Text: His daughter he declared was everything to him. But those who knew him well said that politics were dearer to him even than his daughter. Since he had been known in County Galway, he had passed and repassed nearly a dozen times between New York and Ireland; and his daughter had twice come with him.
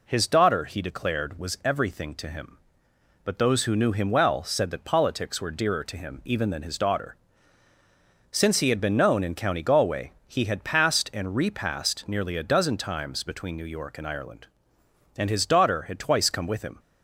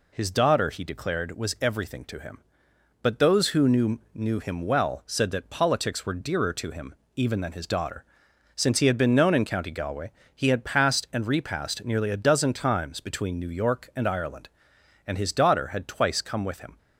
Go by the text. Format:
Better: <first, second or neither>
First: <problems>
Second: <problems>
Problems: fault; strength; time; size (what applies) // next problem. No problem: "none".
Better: first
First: none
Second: says "knew" twice; at 4.1 s // pauses between "him" and "even"; slight; at 6.9 s; 0.22 s long